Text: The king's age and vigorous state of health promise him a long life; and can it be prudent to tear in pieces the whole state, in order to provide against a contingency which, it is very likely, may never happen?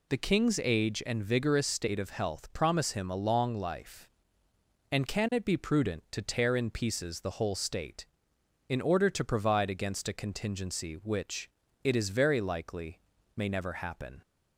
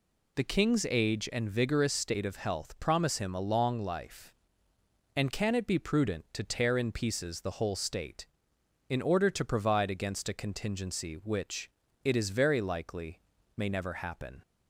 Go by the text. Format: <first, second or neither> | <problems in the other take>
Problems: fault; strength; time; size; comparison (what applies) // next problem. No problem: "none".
neither | none